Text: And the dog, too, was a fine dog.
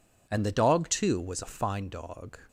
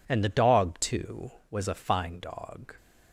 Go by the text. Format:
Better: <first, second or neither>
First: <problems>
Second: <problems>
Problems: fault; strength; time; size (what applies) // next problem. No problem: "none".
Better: neither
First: none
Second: none